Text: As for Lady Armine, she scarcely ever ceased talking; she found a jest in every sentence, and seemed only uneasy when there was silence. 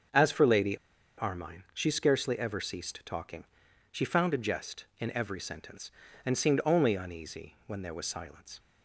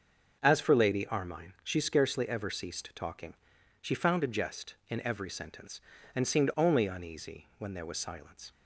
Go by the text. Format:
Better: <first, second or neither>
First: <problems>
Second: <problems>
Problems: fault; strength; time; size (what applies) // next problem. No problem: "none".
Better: second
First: starts louder than the rest; until 1.5 s; 6.5 dB // pauses between "Lady" and "Armine"; at 0.7 s; 0.42 s long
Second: starts louder than the rest; until 1.4 s; 6.5 dB